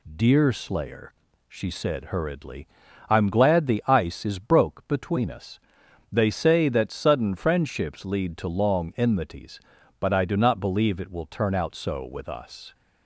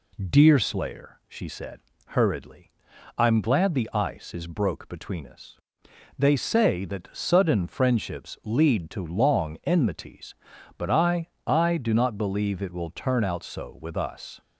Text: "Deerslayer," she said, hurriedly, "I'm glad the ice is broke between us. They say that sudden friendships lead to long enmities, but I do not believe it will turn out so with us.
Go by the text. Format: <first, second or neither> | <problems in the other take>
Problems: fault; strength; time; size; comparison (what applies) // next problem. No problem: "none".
first | says "I" twice; at 11.4 s